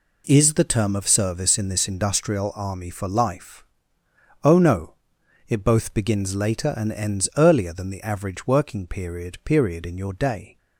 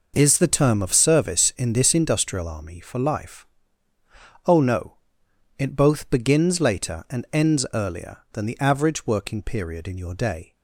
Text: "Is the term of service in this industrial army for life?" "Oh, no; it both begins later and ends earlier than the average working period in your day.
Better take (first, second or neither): second